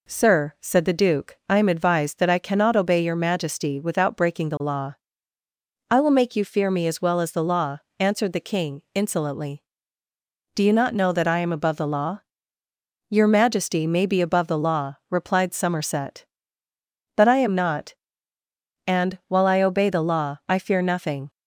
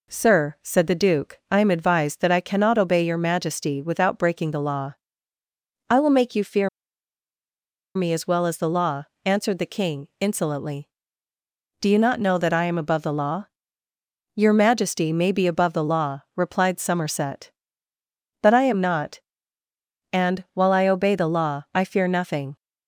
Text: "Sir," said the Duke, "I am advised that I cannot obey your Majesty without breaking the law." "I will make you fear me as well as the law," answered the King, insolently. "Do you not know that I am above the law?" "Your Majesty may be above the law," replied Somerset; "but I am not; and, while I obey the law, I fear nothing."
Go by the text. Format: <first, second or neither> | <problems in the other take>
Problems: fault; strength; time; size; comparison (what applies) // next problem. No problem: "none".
first | pauses between "fear" and "me"; strong; at 6.6 s; 1.2 s long